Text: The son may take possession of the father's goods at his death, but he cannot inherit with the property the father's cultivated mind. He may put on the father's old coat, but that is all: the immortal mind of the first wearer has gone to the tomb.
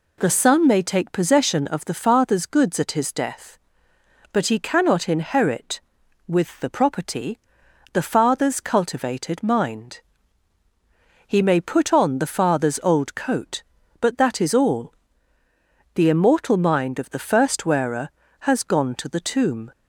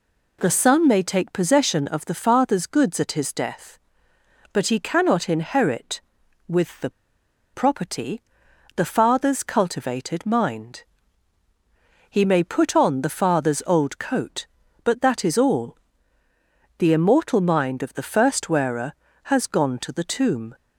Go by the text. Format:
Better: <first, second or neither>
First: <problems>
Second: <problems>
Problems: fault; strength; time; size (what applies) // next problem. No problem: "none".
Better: first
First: pauses between "property" and "the"; noticeable; at 7.3 s; 0.54 s long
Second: pauses between "the" and "property"; noticeable; at 6.8 s; 0.64 s long // pauses between "property" and "the"; noticeable; at 8.2 s; 0.54 s long